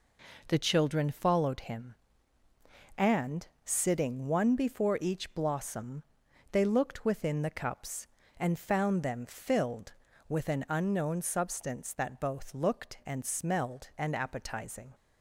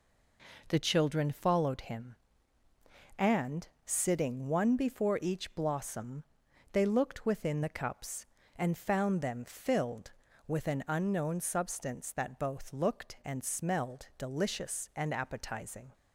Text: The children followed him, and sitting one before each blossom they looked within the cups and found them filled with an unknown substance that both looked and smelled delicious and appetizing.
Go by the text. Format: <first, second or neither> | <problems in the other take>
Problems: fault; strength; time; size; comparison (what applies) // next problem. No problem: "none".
second | pauses between "and" and "sitting"; slight; at 3.4 s; 0.18 s long; slight in the second // pauses between "blossom" and "they"; noticeable; at 6.0 s; 0.50 s long; noticeable in the second // skips "delicious"; at 13.9 s